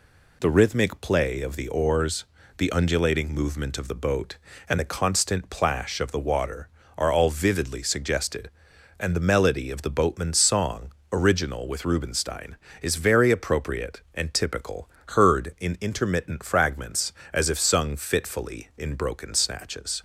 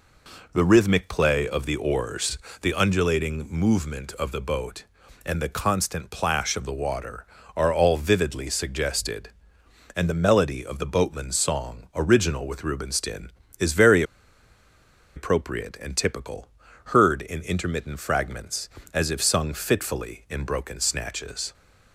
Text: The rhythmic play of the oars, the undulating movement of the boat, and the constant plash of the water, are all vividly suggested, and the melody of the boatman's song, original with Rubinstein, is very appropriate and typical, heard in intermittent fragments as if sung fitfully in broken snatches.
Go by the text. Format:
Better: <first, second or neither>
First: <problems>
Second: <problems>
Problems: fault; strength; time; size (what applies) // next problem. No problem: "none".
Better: first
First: none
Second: pauses between "very" and "appropriate"; at 14.0 s; 1.1 s long